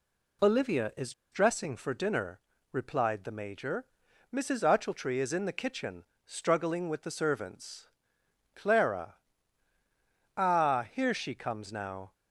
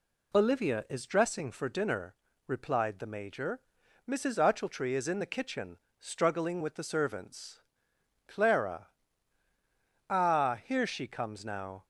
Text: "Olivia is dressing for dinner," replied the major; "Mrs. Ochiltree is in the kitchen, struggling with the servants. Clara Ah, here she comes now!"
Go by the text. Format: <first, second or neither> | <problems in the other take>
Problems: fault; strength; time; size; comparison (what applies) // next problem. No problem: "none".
second | pauses between "is" and "dressing"; slight; at 1.1 s; 0.20 s long // pauses between "Clara" and "Ah"; at 9.1 s; 1.1 s long; also in the second